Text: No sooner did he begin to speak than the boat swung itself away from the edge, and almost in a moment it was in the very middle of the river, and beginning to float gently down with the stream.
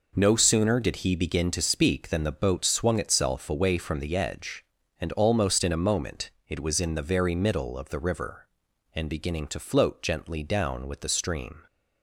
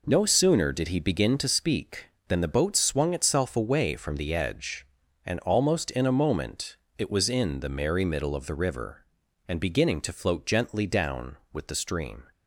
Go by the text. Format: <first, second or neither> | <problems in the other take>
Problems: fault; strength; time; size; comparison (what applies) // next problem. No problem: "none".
first | pauses between "moment" and "it"; slight; at 6.7 s; 0.22 s long; slight in the first // says "merry" for "very"; at 7.7 s